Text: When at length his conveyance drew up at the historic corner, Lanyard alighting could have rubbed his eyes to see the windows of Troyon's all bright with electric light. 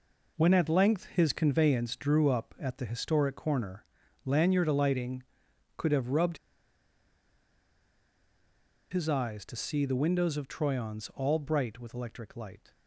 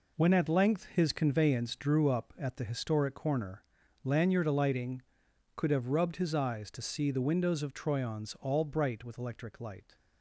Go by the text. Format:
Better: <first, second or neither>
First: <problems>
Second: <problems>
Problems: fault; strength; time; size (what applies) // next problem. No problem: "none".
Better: second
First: pauses between "rubbed" and "his"; strong; at 6.3 s; 2.5 s long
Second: none